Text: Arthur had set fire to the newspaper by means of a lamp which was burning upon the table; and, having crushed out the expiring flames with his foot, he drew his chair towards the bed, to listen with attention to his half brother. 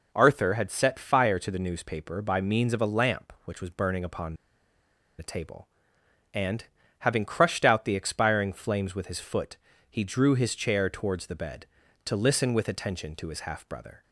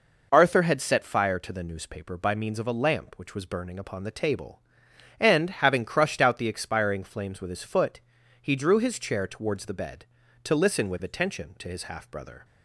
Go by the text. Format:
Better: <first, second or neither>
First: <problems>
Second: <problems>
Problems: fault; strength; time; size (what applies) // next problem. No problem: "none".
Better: second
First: pauses between "upon" and "the"; noticeable; at 4.3 s; 0.84 s long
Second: none